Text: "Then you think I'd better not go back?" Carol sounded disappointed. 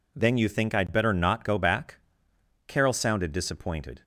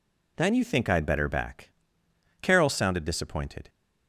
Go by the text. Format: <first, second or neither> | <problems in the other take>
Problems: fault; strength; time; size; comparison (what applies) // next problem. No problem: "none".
first | skips "not go"; at 1.2 s